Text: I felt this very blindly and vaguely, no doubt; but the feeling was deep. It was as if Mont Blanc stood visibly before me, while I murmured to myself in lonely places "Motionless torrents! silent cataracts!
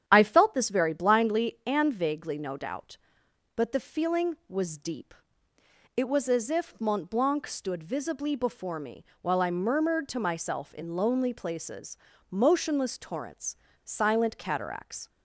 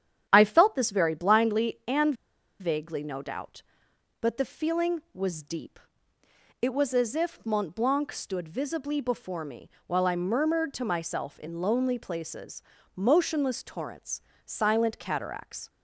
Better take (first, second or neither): first